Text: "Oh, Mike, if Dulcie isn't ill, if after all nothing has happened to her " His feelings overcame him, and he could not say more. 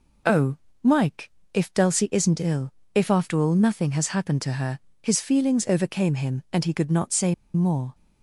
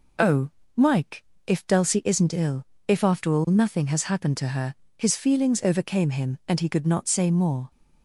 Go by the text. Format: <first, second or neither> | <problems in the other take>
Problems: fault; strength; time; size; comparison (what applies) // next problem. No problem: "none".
second | pauses between "say" and "more"; slight; at 7.3 s; 0.20 s long